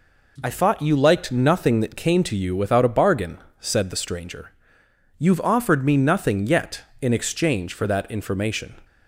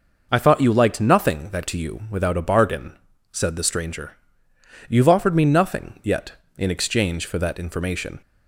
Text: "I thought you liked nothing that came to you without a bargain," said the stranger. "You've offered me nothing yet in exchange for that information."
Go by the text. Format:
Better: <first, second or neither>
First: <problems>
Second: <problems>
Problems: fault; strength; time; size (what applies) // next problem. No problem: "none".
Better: first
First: none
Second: skips "came"; at 1.6 s